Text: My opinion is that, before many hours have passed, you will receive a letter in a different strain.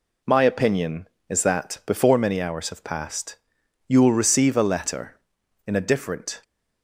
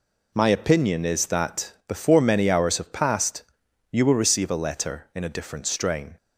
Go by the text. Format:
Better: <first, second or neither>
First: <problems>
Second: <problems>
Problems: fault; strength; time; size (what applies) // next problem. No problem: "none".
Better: second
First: stops before "strain"; at 6.4 s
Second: none